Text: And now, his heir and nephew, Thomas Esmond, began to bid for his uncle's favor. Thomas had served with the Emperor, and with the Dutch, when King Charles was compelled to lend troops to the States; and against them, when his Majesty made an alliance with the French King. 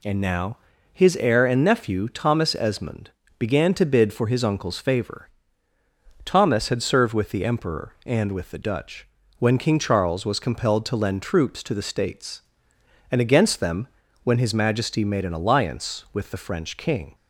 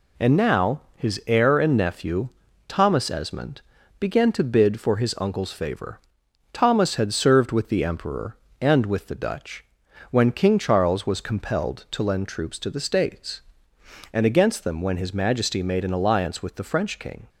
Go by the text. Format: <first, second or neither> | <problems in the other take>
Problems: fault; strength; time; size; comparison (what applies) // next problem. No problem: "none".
neither | none